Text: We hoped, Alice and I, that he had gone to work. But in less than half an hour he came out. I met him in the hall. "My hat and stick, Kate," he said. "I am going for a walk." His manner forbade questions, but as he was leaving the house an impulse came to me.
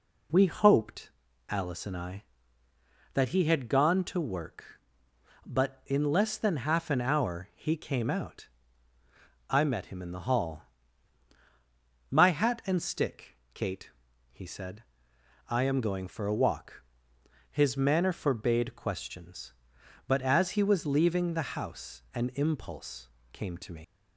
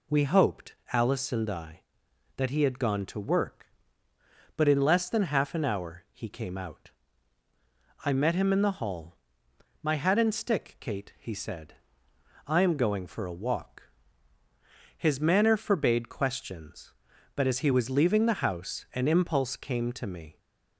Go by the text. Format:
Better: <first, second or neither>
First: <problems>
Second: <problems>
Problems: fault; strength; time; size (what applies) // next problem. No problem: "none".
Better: second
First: pauses between "impulse" and "came"; slight; at 23.0 s; 0.24 s long // leaves "me" unfinished; at 23.8 s; 115 ms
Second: none